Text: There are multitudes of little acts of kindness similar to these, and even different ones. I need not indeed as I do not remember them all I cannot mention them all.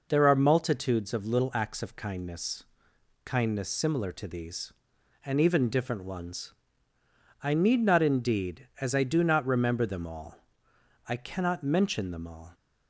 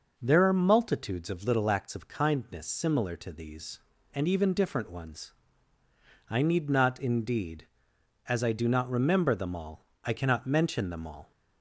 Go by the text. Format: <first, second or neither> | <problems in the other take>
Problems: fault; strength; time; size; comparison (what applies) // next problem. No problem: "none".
second | says "kindness" twice; at 3.2 s // pauses between "all" and "I"; noticeable; at 10.3 s; 0.72 s long; slight in the second